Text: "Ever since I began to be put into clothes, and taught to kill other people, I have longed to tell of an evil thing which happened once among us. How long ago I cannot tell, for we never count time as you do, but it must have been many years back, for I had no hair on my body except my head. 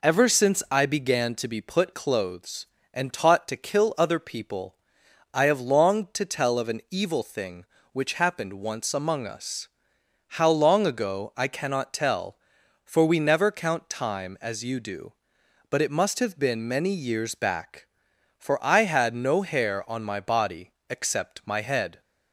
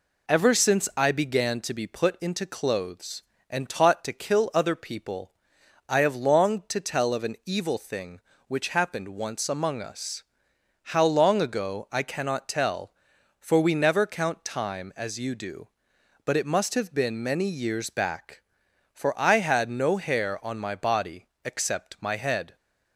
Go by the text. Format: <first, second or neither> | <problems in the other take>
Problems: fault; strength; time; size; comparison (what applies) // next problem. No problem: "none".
second | skips "into"; at 1.9 s // pauses between "body" and "except"; slight; at 20.7 s; 0.16 s long; slight in the second